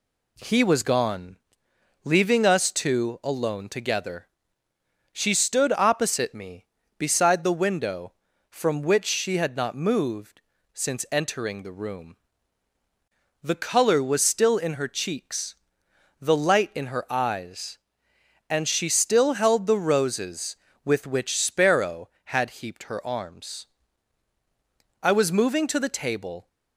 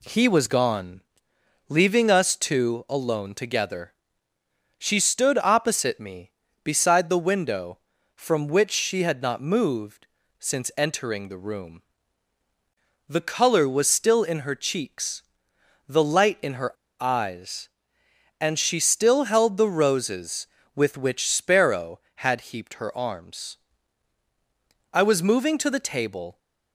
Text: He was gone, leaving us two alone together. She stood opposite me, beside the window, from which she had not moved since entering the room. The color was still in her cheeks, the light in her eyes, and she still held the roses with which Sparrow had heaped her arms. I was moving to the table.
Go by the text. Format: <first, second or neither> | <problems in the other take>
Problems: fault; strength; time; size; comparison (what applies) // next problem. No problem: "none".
first | pauses between "moved" and "since"; slight; at 10.0 s; 0.32 s long; slight in the first // pauses between "her" and "eyes"; slight; at 16.7 s; 0.26 s long